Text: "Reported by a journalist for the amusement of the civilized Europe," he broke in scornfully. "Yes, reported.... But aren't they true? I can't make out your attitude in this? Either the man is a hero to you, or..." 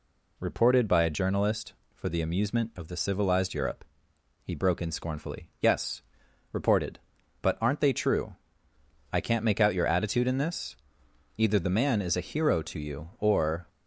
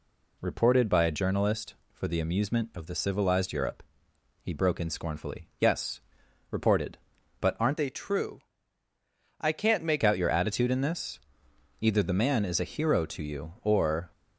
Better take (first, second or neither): first